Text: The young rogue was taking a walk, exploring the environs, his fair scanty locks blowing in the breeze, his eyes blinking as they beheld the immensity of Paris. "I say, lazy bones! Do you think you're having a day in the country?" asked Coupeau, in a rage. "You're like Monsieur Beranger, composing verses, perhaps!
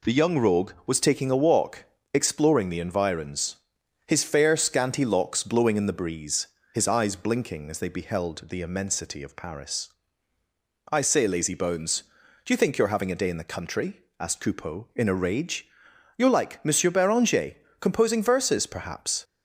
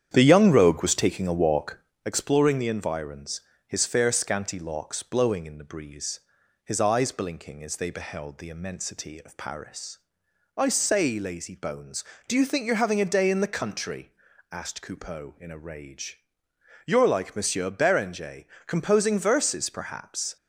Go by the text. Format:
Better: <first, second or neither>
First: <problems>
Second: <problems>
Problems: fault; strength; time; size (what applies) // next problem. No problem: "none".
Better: first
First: none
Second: starts louder than the rest; strong; until 2.0 s; 9 dB